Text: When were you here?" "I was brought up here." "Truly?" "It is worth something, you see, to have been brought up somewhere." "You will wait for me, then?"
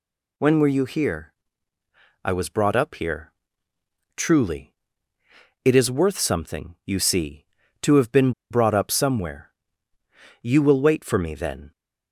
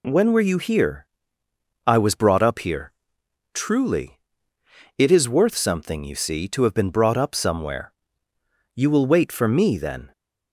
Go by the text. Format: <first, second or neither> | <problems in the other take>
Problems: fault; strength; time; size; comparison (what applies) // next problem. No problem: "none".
second | pauses between "been" and "brought"; slight; at 8.3 s; 0.18 s long